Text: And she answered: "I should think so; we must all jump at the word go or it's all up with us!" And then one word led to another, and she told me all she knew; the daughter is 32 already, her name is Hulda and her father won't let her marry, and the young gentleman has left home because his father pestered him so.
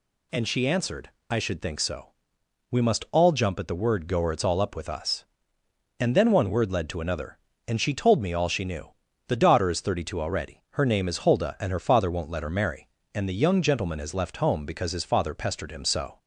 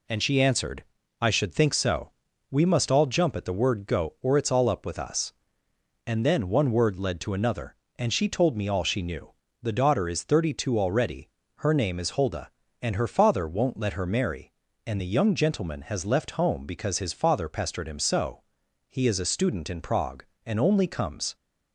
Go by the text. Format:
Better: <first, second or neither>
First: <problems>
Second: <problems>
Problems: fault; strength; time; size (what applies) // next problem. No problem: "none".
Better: first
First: none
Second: goes on to say "He is a student in Prague and only comes"; strong; from 18.8 s on; 2.4 s long